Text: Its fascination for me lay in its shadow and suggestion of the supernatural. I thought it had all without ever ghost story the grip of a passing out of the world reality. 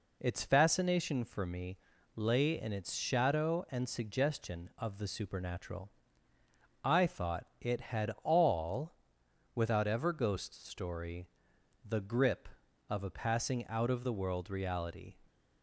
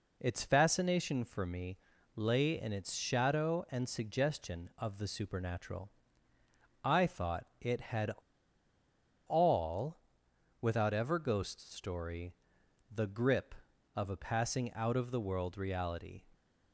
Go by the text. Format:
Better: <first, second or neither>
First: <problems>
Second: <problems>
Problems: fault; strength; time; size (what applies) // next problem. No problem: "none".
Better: first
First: pauses between "me" and "lay"; at 1.7 s; 0.38 s long // pauses between "all" and "without"; noticeable; at 8.9 s; 0.60 s long // pauses between "story" and "the"; noticeable; at 11.2 s; 0.56 s long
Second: pauses between "me" and "lay"; at 1.7 s; 0.38 s long // pauses between "had" and "all"; at 8.1 s; 1.1 s long // pauses between "all" and "without"; noticeable; at 9.9 s; 0.62 s long // pauses between "story" and "the"; noticeable; at 12.3 s; 0.56 s long